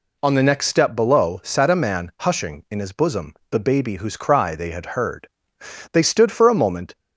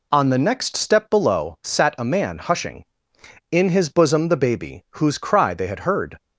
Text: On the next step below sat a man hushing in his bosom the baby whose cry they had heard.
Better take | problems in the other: second | pauses between "bosom" and "the"; slight; at 3.3 s; 0.16 s long // goes on to say "They stood for a moment"; noticeable; from 5.9 s on; 1.0 s long

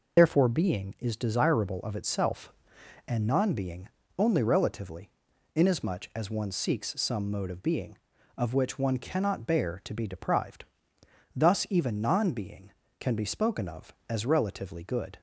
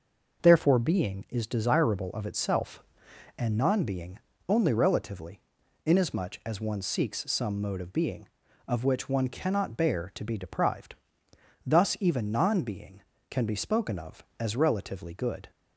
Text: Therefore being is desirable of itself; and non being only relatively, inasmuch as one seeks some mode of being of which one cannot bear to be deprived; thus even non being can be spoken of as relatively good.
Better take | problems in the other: second | loses the start of "Therefore"; at 0.1 s; 55 ms // pauses between "being" and "only"; slight; at 3.8 s; 0.28 s long; slight in the second

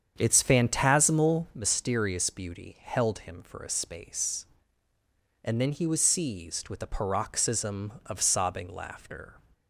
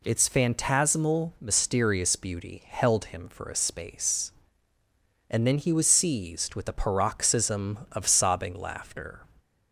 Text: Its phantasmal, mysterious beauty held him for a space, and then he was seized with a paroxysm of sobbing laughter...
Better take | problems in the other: second | starts louder than the rest; strong; until 1.7 s; 7.5 dB

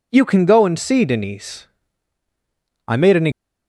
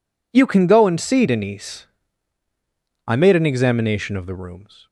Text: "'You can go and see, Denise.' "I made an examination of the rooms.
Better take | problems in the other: second | stops before "examination of the rooms"; at 3.3 s

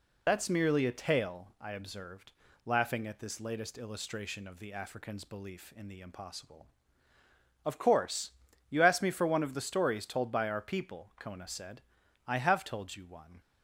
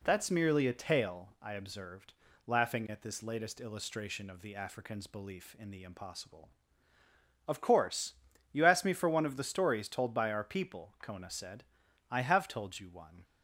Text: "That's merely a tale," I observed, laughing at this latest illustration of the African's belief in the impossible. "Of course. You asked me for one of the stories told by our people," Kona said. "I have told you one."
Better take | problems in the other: second | loses the start of "That's"; at 0.2 s; 65 ms

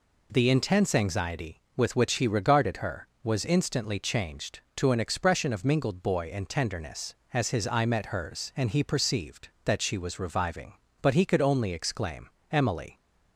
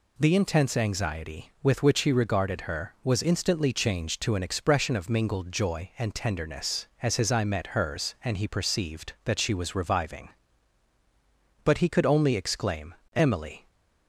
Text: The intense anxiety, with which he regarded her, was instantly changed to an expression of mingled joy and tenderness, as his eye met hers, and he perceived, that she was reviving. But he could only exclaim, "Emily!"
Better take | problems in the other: second | says "boy" for "joy"; at 6.0 s

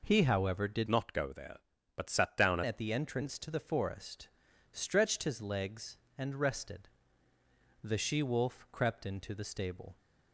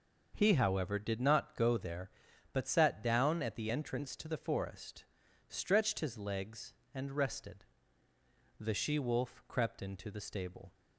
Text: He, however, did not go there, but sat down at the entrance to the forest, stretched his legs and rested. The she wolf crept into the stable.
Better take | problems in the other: second | changes voice from "not" to "down"; from 0.8 to 2.6 s; 1.8 s long

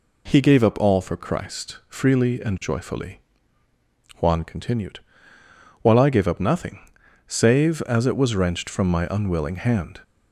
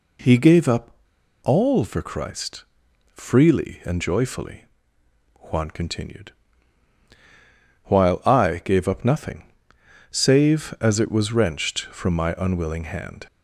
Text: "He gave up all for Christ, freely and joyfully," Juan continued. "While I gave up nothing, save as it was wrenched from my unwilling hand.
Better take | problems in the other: first | pauses between "up" and "all"; noticeable; at 0.9 s; 0.52 s long

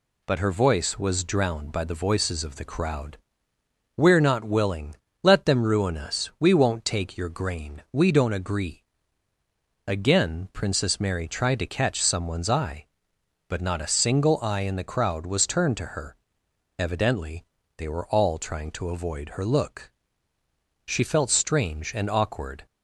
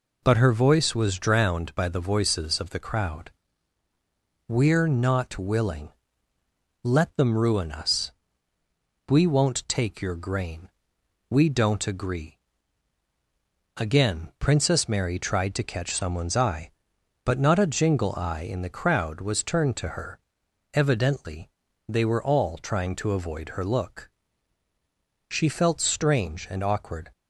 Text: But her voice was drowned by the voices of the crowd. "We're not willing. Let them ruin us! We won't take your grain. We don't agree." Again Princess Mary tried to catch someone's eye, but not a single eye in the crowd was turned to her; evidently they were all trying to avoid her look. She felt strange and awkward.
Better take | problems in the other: first | says "jingle" for "single"; at 17.6 s // pauses between "evidently" and "they"; at 21.5 s; 0.38 s long; slight in the first

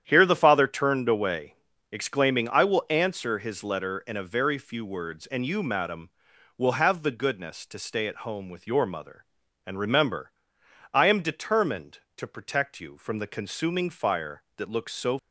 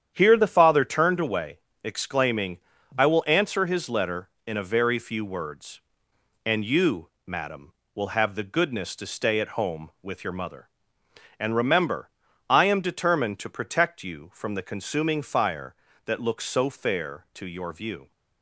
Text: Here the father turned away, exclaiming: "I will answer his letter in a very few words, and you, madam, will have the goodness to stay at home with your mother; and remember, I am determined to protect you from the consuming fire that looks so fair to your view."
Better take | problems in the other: second | starts louder than the rest; strong; until 1.0 s; 9.5 dB; strong in the second // stops before "fair to your view"; at 15.1 s

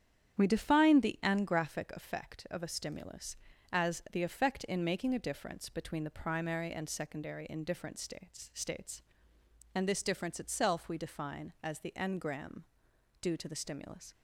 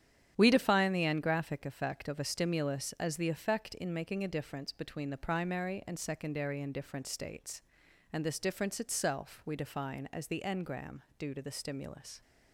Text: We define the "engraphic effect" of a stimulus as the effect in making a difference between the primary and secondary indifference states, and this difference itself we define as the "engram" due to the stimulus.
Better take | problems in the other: second | starts louder than the rest; strong; until 1.4 s; 9.5 dB; strong in the second // says "states" twice; at 8.5 s // pauses between "engram" and "due"; noticeable; at 12.6 s; 0.58 s long; slight in the second

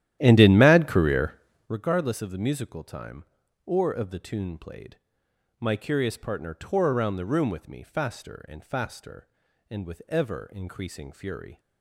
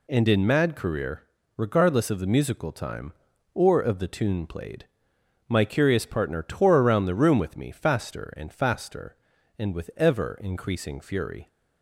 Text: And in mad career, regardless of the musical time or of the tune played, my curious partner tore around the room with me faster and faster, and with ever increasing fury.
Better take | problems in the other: second | starts louder than the rest; strong; until 1.8 s; 12.5 dB

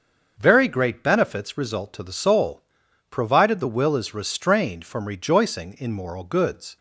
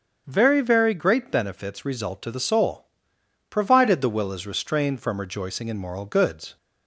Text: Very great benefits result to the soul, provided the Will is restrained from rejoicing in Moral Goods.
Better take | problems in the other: first | starts louder than the rest; until 1.2 s; 7 dB; also in the first // says "Very" twice; at 0.6 s

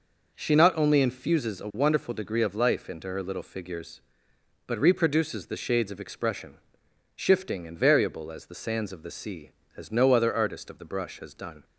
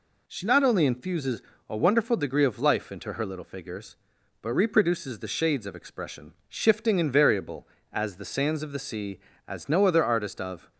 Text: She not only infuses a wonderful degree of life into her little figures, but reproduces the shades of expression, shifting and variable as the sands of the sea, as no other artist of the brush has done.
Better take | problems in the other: first | pauses between "infuses" and "a"; slight; at 1.4 s; 0.26 s long // stops before "the brush has done"; at 10.7 s

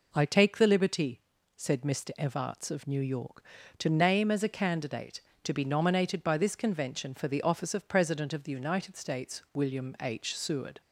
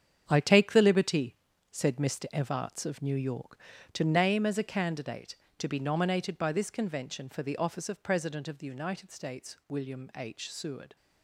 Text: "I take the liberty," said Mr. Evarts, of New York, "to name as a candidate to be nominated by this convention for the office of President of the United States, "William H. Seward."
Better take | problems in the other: first | gets quieter; strong; throughout; 10.5 dB

